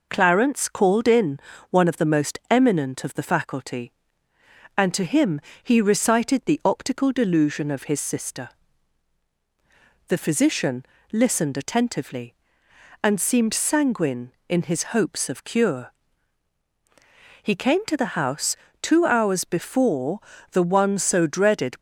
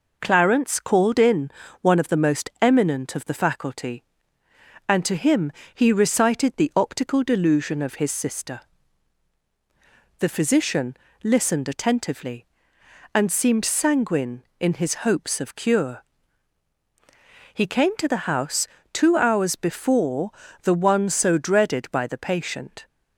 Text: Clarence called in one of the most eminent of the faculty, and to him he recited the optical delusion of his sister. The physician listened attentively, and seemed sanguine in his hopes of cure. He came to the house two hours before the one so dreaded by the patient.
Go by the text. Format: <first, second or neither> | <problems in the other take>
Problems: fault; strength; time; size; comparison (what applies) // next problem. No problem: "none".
second | pauses between "in" and "one"; slight; at 1.3 s; 0.32 s long; slight in the second // pauses between "him" and "he"; slight; at 5.3 s; 0.22 s long; slight in the second // pauses between "physician" and "listened"; slight; at 10.8 s; 0.26 s long; slight in the second // pauses between "house" and "two"; slight; at 18.5 s; 0.26 s long; slight in the second // pauses between "before" and "the"; slight; at 20.1 s; 0.32 s long; slight in the second // stops before "by the patient"; at 21.7 s